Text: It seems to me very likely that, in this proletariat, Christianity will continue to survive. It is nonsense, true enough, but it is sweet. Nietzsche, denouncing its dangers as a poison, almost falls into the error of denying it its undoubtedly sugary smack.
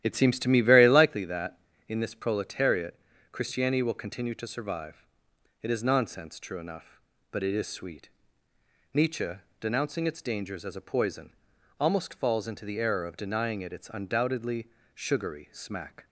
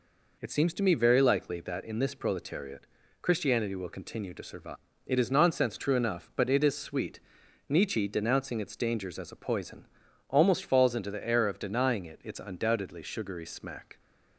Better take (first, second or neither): second